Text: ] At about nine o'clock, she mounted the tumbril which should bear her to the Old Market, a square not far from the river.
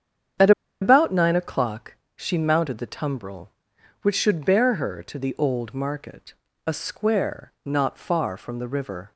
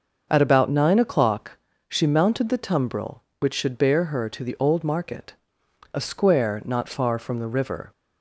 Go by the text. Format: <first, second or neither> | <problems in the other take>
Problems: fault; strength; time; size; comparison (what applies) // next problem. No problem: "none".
second | starts louder than the rest; strong; until 1.7 s; 8 dB // pauses between "At" and "about"; slight; at 0.5 s; 0.29 s long